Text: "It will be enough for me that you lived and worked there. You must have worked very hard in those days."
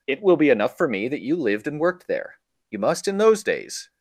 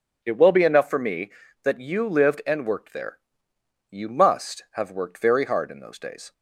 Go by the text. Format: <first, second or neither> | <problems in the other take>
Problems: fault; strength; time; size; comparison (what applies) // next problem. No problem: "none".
second | skips "have worked very hard"; at 3.0 s